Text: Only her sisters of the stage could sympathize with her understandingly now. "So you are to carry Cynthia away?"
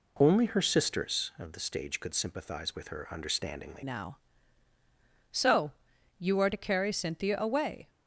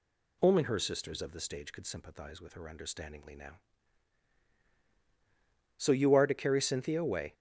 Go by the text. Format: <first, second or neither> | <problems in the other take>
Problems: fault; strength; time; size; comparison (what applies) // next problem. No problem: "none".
second | changes voice at "now"; from 3.8 s on; 4.0 s long // pauses between "So" and "you"; noticeable; at 5.7 s; 0.48 s long